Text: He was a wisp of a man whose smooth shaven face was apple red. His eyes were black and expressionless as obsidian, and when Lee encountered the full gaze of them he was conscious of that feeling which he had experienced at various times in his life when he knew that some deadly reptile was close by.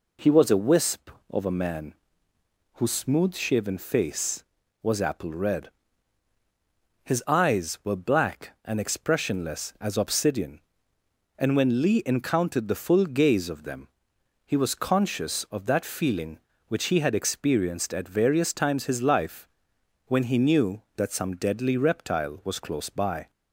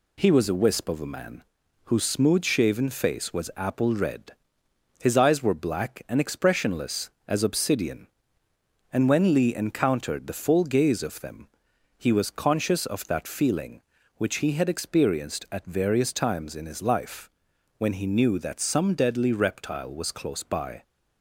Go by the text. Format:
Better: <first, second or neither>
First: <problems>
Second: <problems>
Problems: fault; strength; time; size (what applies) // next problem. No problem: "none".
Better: second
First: pauses between "man" and "whose"; noticeable; at 1.9 s; 0.80 s long // pauses between "them" and "he"; noticeable; at 13.8 s; 0.58 s long // skips "in"; at 18.8 s // pauses between "life" and "when"; noticeable; at 19.4 s; 0.60 s long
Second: pauses between "man" and "whose"; at 1.4 s; 0.40 s long // pauses between "them" and "he"; noticeable; at 11.4 s; 0.50 s long // pauses between "life" and "when"; noticeable; at 17.3 s; 0.46 s long